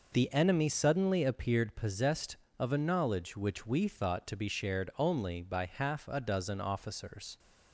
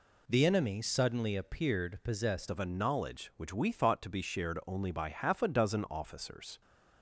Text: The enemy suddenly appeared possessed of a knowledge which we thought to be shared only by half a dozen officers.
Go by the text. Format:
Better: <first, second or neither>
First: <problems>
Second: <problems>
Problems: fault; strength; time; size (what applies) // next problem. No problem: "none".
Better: first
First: none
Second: changes voice at "of"; from 2.5 s on; 4.1 s long